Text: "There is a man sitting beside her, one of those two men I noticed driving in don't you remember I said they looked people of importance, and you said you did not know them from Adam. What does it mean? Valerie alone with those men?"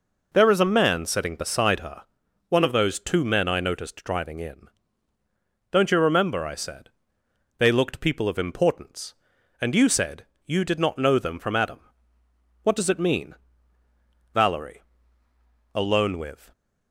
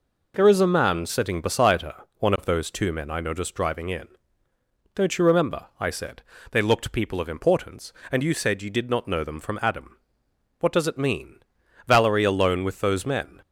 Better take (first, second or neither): second